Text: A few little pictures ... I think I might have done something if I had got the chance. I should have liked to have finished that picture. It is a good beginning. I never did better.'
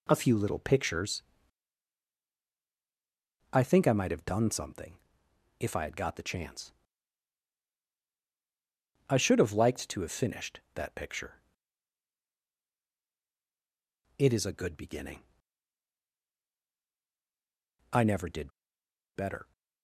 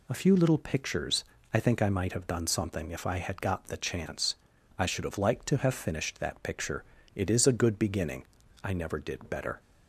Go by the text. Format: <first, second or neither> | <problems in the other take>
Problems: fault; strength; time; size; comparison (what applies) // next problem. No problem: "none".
second | pauses between "something" and "if"; noticeable; at 4.9 s; 0.62 s long // pauses between "did" and "better"; noticeable; at 18.5 s; 0.64 s long